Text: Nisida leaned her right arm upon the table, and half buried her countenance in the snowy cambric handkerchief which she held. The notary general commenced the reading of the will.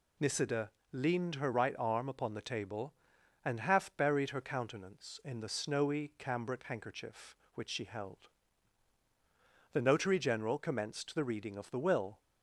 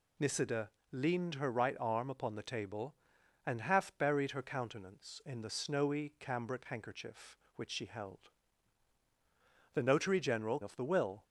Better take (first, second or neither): first